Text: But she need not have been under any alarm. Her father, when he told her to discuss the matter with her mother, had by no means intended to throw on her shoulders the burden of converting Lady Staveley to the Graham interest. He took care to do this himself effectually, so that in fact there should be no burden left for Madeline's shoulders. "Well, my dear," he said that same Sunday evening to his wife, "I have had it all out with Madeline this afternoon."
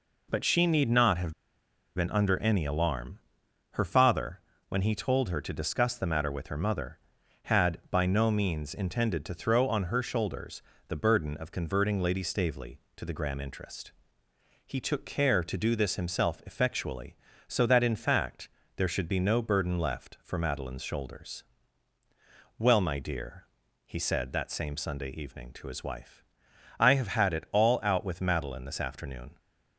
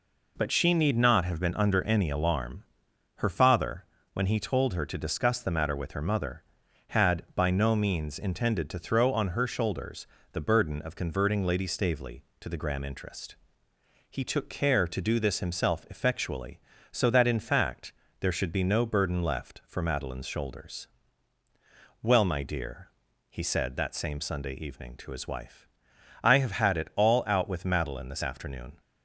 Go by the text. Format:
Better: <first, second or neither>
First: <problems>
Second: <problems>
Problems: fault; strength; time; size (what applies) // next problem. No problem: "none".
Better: second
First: pauses between "have" and "been"; noticeable; at 1.3 s; 0.62 s long // pauses between "shoulders" and "the"; slight; at 10.6 s; 0.26 s long // pauses between "fact" and "there"; slight; at 18.4 s; 0.28 s long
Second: pauses between "shoulders" and "the"; slight; at 10.0 s; 0.26 s long // pauses between "fact" and "there"; slight; at 17.9 s; 0.28 s long